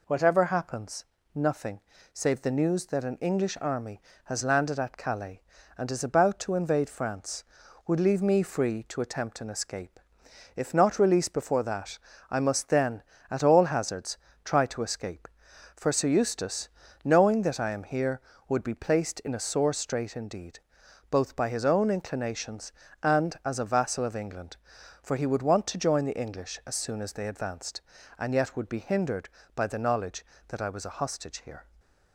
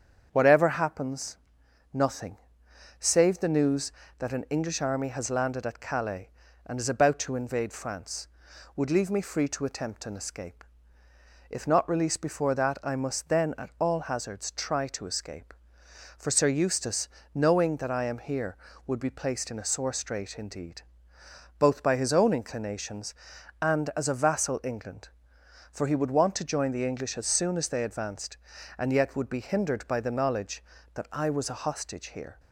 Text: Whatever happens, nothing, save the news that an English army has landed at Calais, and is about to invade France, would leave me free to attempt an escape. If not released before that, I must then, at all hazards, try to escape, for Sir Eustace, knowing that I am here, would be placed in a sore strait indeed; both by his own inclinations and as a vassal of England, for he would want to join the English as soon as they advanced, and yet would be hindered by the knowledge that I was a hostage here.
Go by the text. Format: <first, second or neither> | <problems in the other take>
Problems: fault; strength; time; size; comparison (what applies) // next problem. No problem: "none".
first | starts louder than the rest; strong; until 1.3 s; 7.5 dB // skips "of"; at 24.6 s